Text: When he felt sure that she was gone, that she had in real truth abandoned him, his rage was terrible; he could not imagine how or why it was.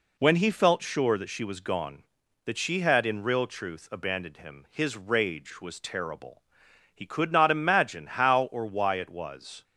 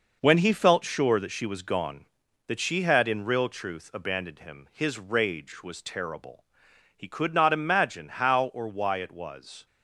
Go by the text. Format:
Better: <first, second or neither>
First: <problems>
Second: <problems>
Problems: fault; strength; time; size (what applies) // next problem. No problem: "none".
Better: first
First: none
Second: gets quieter; strong; throughout; 8 dB